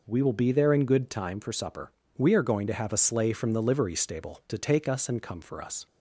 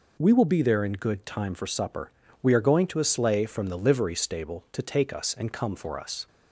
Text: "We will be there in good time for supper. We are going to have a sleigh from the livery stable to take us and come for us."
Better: first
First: none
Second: skips "have"; at 2.9 s

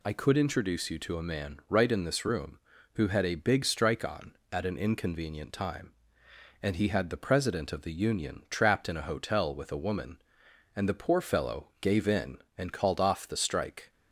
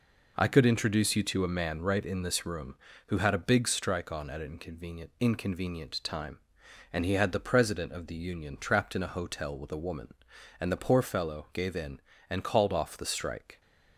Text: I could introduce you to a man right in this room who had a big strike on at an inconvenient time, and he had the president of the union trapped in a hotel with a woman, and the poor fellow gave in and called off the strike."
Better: first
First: none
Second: says "inconvenient" twice; at 5.2 s

